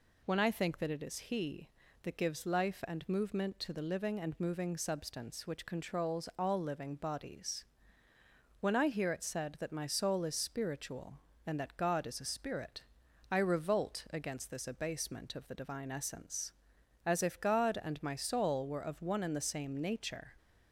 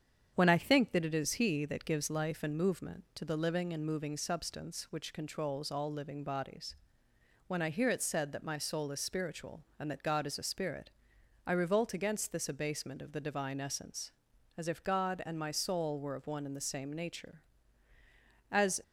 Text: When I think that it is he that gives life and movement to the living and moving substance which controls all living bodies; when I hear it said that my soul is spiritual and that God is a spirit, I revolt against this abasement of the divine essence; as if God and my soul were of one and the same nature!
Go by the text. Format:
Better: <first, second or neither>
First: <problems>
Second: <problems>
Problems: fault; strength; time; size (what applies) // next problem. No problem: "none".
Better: first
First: none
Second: starts louder than the rest; strong; until 1.3 s; 8 dB // goes on to say "As"; slight; from 18.5 s on; 0.32 s long